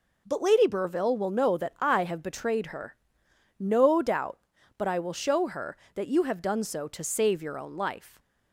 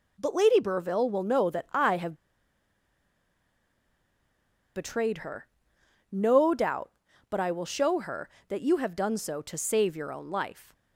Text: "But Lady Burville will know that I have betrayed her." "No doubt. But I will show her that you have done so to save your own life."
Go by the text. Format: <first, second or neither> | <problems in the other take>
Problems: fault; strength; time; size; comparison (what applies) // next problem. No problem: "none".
first | pauses between "have" and "betrayed"; strong; at 2.1 s; 2.6 s long